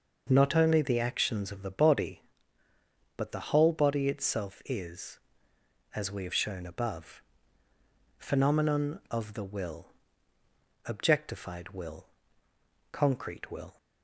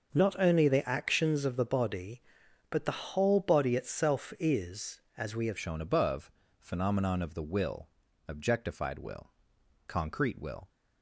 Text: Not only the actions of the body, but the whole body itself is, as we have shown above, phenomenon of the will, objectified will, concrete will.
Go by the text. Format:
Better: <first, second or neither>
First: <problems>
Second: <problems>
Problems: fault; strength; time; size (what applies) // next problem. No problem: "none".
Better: first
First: none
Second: starts louder than the rest; until 1.2 s; 6.5 dB // changes voice at "shown"; from 5.5 s on; 5.1 s long